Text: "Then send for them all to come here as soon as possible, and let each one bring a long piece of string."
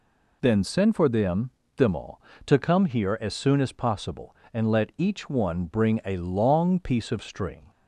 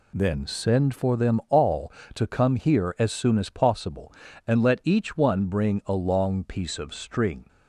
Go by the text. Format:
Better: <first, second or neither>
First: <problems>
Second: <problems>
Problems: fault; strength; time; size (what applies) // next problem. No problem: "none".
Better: second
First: says "them" twice; at 1.7 s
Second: none